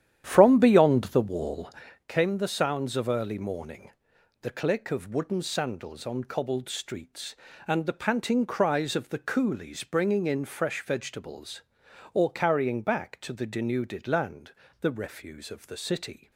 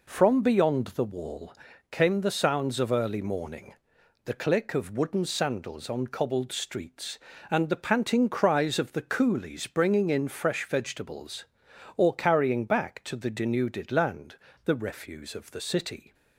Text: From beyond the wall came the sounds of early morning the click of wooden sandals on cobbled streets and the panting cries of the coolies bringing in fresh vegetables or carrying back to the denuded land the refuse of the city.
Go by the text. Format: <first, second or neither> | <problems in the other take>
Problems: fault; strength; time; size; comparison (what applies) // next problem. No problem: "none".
second | starts louder than the rest; strong; until 2.1 s; 10 dB // pauses between "wall" and "came"; at 1.6 s; 0.38 s long; also in the second // pauses between "morning" and "the"; noticeable; at 3.9 s; 0.50 s long; noticeable in the second // pauses between "land" and "the"; slight; at 14.5 s; 0.28 s long; slight in the second